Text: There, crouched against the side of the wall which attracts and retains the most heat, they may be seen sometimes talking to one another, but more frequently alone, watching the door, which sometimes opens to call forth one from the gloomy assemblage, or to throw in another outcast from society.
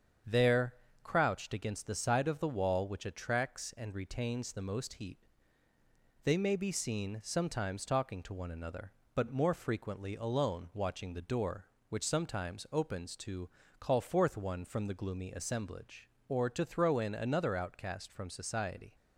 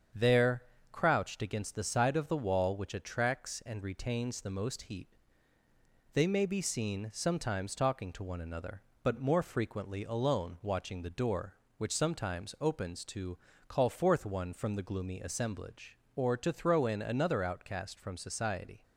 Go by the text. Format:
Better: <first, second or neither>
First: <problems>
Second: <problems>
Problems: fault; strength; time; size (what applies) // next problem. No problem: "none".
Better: neither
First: starts louder than the rest; strong; until 1.5 s; 7.5 dB // pauses between "to" and "call"; slight; at 13.4 s; 0.32 s long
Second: starts louder than the rest; strong; until 1.4 s; 7.5 dB // pauses between "to" and "call"; slight; at 13.3 s; 0.32 s long